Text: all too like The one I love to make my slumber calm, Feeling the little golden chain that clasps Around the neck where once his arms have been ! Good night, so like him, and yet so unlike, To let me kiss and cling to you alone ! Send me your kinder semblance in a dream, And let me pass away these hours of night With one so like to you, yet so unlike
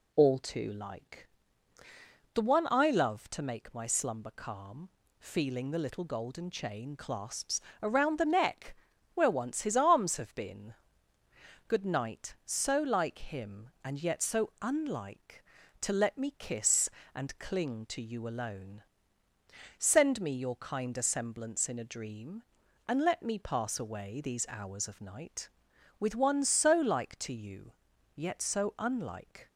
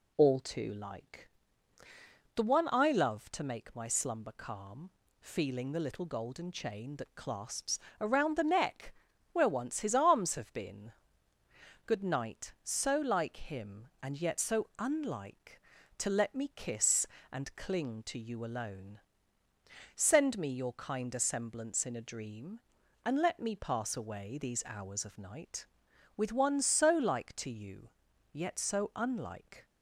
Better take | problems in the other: second | pauses between "like" and "The"; at 1.2 s; 1.0 s long; also in the second // skips "that"; at 6.9 s // pauses between "clasps" and "Around"; slight; at 7.5 s; 0.22 s long; slight in the second // pauses between "neck" and "where"; at 8.7 s; 0.40 s long; also in the second

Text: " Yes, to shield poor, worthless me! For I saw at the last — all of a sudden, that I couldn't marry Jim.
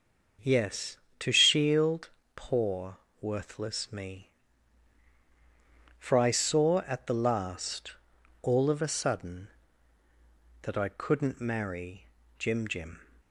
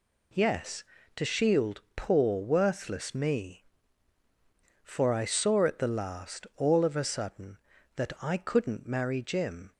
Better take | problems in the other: second | starts louder than the rest; until 1.6 s; 6.5 dB // pauses between "shield" and "poor"; slight; at 2.0 s; 0.26 s long // pauses between "marry" and "Jim"; slight; at 12.0 s; 0.32 s long // says "Jim" twice; at 12.6 s

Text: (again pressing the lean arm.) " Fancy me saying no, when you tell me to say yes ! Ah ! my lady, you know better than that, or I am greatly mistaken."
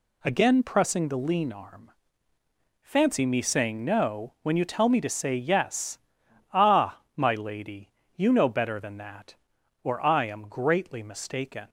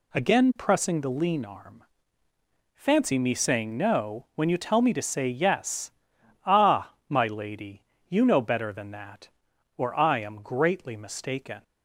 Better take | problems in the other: neither | none

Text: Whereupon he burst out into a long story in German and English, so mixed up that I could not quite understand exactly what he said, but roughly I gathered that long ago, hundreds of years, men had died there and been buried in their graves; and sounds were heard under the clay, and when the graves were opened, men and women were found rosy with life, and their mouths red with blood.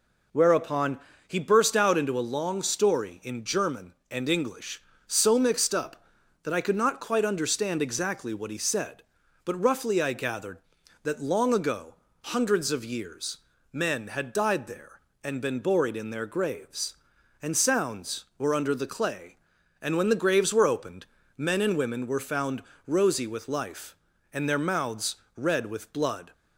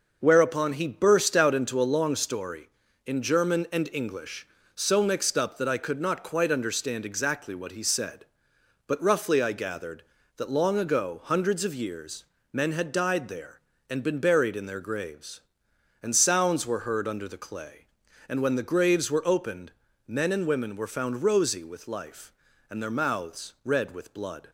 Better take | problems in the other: second | pauses between "Whereupon" and "he"; slight; at 0.9 s; 0.28 s long // skips "heard"; at 18.5 s // pauses between "found" and "rosy"; slight; at 22.6 s; 0.24 s long // pauses between "mouths" and "red"; slight; at 25.1 s; 0.20 s long

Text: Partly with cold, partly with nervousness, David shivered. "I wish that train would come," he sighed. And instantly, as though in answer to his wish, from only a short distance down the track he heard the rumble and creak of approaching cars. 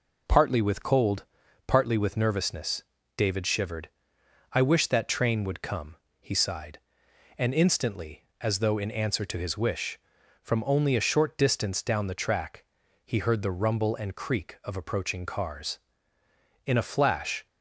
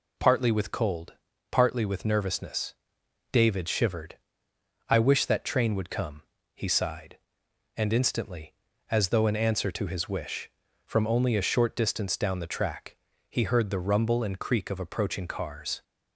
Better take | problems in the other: second | pauses between "track" and "he"; at 12.6 s; 0.40 s long; slight in the second // goes on to say "In a flash"; noticeable; from 16.6 s on; 0.80 s long

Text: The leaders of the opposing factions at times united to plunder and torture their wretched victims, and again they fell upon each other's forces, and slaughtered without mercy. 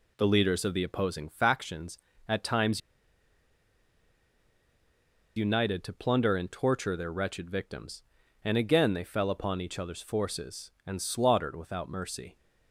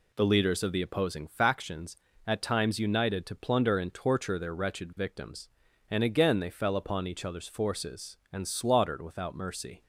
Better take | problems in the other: second | pauses between "times" and "united"; strong; at 2.7 s; 2.5 s long

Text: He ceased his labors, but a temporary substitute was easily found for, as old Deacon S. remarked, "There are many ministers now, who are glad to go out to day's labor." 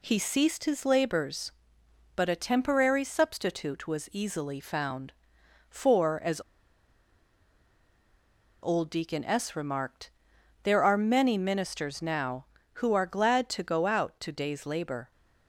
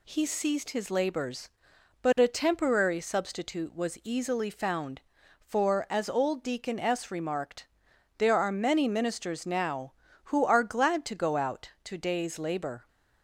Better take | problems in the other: second | pauses between "as" and "old"; strong; at 6.4 s; 2.2 s long

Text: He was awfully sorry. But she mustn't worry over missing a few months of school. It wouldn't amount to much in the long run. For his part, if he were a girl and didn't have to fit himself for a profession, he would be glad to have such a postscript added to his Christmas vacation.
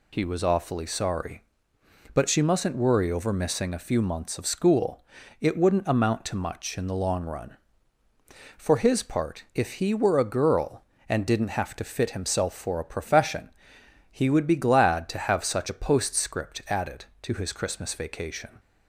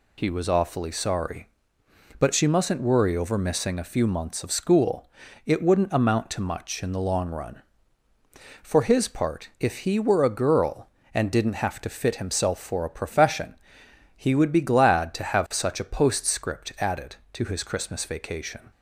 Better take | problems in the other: neither | none

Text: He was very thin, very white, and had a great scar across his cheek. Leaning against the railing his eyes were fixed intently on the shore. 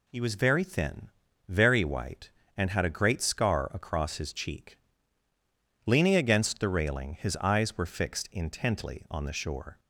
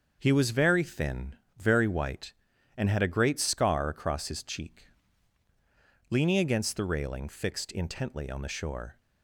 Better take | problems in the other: first | starts louder than the rest; until 1.2 s; 6.5 dB // skips "his eyes were"; at 7.2 s

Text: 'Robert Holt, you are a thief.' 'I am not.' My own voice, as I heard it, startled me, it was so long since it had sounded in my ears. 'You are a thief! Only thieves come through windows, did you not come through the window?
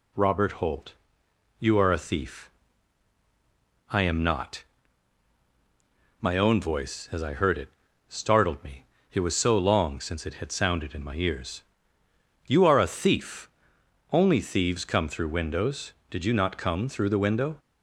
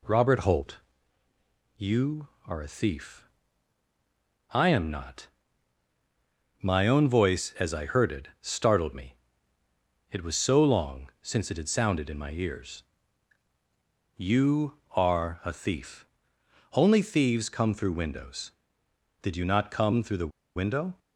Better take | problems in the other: first | pauses between "the" and "window"; slight; at 20.3 s; 0.27 s long

